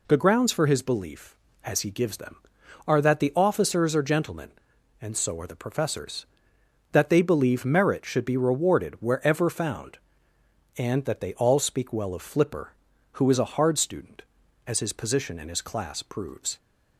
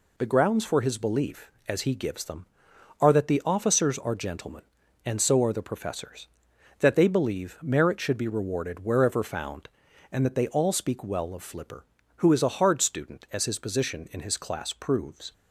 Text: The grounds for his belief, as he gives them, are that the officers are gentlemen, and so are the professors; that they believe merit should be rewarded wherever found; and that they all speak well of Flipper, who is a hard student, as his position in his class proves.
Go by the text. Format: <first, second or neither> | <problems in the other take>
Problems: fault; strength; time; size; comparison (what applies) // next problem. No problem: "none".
neither | none